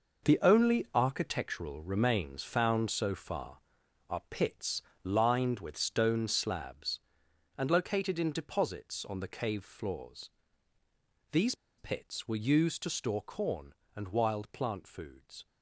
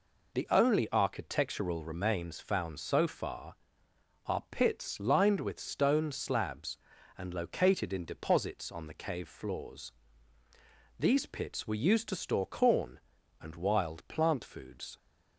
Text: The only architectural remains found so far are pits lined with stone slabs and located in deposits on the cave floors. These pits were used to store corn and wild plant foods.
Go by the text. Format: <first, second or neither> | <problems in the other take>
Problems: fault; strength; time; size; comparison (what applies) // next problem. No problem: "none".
second | pauses between "pits" and "lined"; slight; at 4.8 s; 0.24 s long // pauses between "These" and "pits"; slight; at 11.5 s; 0.23 s long